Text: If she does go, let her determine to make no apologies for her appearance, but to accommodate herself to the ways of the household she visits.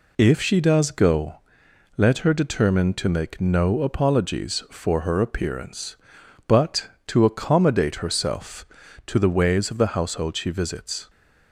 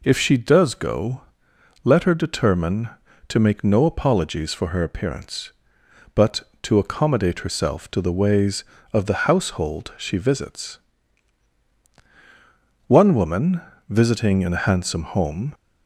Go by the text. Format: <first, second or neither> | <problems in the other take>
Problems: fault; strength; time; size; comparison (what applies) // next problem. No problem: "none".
first | goes on to say "One woman visiting in a handsome home"; strong; from 12.8 s on; 2.6 s long